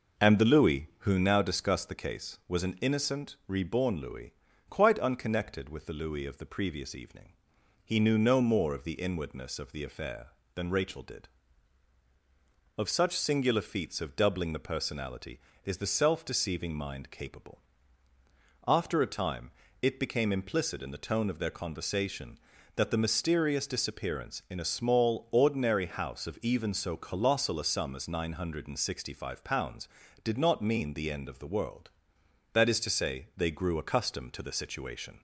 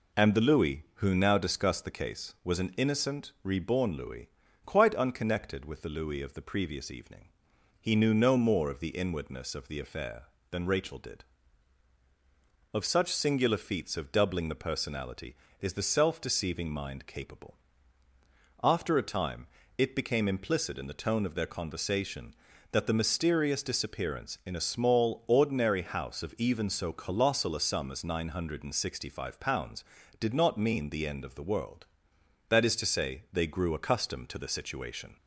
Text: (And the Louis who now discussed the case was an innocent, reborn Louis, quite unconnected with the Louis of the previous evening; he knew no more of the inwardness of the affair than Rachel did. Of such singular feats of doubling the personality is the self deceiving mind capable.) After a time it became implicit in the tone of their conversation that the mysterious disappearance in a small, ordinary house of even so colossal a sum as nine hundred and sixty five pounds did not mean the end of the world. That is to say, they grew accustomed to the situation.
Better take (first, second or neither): second